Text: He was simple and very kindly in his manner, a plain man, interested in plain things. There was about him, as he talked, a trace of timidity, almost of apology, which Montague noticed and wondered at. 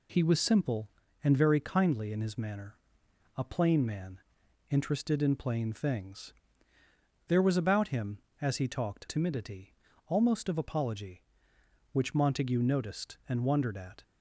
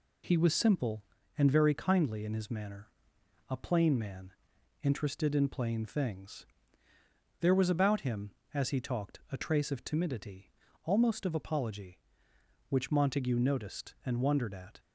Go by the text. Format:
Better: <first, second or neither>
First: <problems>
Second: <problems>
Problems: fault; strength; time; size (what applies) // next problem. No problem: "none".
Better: second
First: skips "a trace of"; at 9.0 s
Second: none